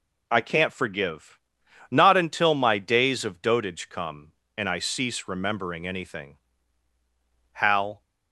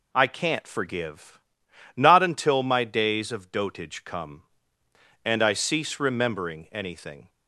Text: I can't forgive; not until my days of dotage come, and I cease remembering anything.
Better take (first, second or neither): second